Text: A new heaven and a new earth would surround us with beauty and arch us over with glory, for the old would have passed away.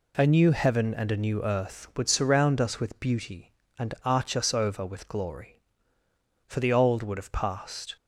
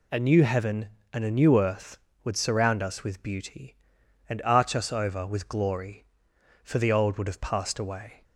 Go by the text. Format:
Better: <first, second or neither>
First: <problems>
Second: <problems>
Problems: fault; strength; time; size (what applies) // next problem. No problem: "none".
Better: second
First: stops before "away"; at 7.9 s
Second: none